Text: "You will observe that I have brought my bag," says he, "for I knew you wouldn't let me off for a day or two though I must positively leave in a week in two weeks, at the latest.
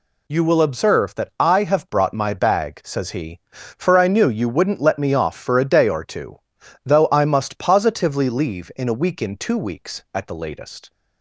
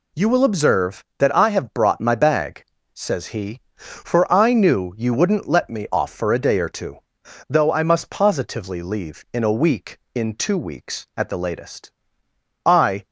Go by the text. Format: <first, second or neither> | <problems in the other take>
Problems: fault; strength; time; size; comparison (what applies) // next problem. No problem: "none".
first | pauses between "two" and "though"; noticeable; at 6.9 s; 0.52 s long; noticeable in the first // goes on to say "I"; slight; from 12.6 s on; 0.42 s long